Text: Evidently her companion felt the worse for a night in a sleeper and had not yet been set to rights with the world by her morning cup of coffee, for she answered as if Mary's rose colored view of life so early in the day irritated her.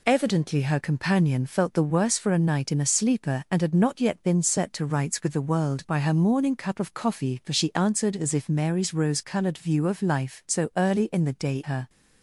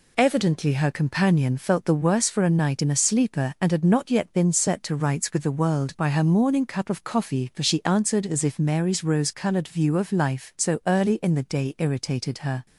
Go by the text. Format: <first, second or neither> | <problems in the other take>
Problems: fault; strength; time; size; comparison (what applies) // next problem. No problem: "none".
second | skips "irritated"; at 11.6 s